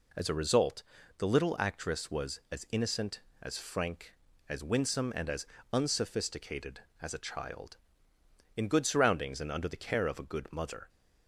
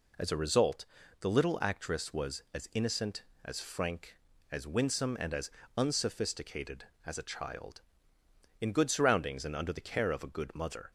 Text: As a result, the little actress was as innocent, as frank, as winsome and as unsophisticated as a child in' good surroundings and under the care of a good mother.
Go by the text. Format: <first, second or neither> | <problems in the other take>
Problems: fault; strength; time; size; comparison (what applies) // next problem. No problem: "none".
neither | pauses between "as" and "unsophisticated"; slight; the same in both